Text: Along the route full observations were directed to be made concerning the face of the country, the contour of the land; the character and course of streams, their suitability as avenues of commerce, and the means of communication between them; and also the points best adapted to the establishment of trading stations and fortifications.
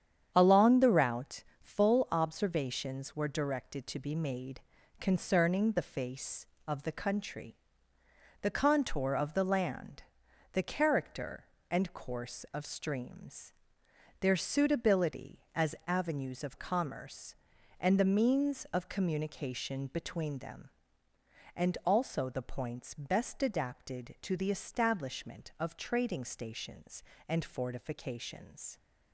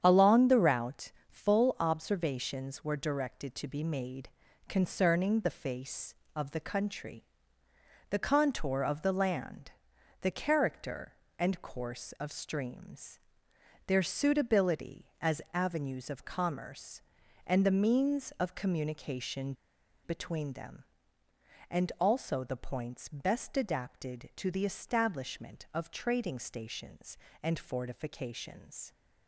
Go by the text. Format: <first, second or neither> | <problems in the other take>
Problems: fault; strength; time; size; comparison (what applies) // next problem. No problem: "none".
first | starts louder than the rest; strong; until 1.0 s; 8.5 dB; strong in the first // pauses between "route" and "full"; slight; at 1.1 s; 0.16 s long; slight in the first // pauses between "made" and "concerning"; at 4.2 s; 0.40 s long; also in the first // pauses between "communication" and "between"; noticeable; at 19.5 s; 0.50 s long